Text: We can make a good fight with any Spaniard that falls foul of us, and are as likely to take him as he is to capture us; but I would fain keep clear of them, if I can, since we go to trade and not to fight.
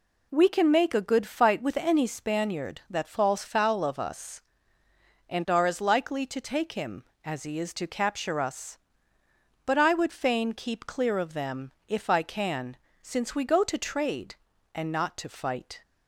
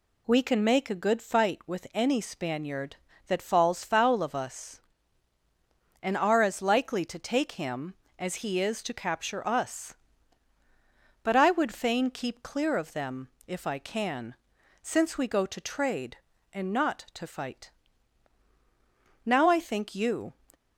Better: first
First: none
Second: goes on to say "Now I think you"; noticeable; from 19.2 s on; 1.0 s long

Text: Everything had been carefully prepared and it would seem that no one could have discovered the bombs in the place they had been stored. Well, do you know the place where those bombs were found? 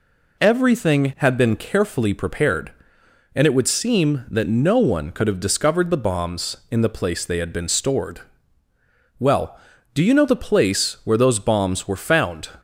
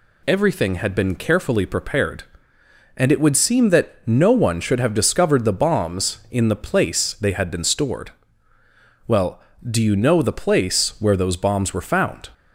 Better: first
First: none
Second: says "should" for "could"; at 4.5 s

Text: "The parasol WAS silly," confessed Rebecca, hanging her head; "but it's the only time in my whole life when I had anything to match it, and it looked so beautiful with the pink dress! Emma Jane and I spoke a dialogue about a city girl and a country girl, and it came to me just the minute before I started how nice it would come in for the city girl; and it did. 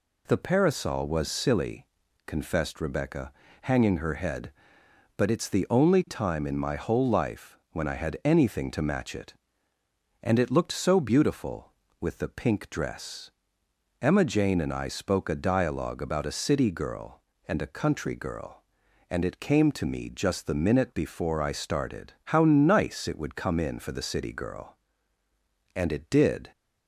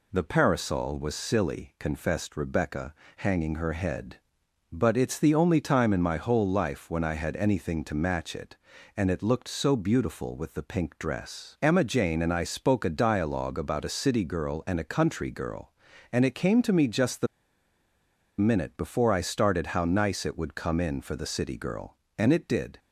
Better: first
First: none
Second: pauses between "the" and "minute"; at 17.2 s; 1.1 s long

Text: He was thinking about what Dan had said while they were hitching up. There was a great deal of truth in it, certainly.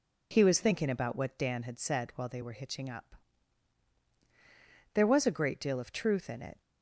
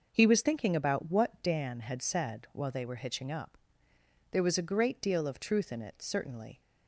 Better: second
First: stops before "certainly"; at 6.6 s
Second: none

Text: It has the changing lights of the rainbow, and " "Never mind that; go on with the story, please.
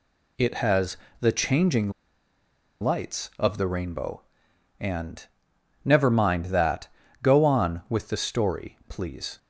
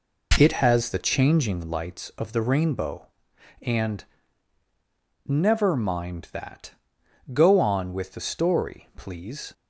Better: second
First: pauses between "has" and "the"; slight; at 0.9 s; 0.22 s long // pauses between "changing" and "lights"; noticeable; at 1.8 s; 0.91 s long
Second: none

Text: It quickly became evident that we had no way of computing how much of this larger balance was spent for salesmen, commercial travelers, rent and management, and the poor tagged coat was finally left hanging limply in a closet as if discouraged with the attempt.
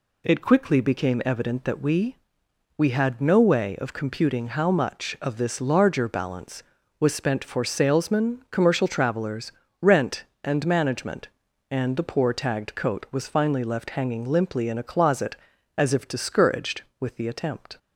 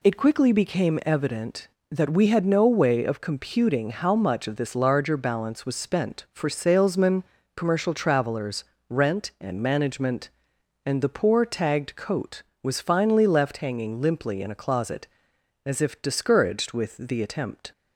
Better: second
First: says "we" twice; at 2.7 s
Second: none

